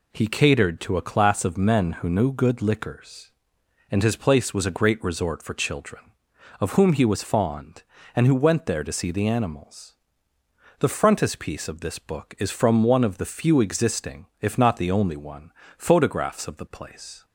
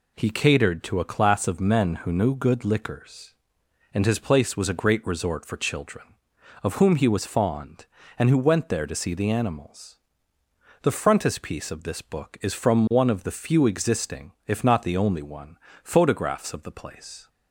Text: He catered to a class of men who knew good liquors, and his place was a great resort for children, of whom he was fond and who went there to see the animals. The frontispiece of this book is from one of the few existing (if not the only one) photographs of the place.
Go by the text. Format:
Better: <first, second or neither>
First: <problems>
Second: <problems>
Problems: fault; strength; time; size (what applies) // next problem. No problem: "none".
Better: neither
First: none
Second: none